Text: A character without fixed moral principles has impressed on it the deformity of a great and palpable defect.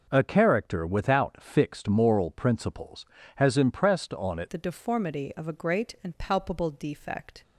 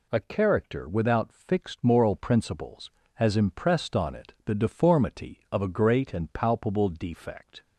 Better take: second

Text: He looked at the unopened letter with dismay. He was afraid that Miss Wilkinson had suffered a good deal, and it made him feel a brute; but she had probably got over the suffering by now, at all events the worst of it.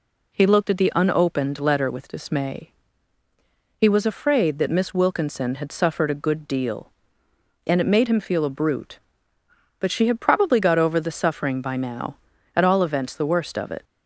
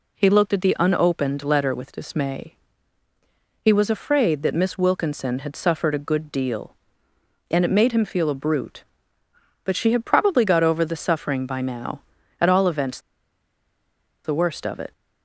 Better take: first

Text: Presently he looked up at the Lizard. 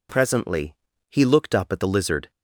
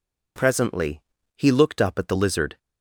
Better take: neither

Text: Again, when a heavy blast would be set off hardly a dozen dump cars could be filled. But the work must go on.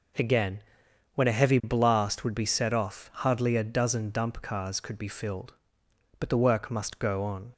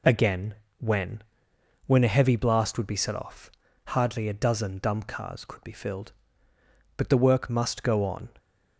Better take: first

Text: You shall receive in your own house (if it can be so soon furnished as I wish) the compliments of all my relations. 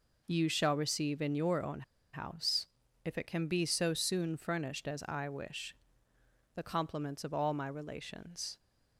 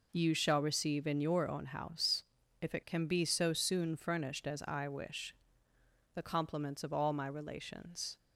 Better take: second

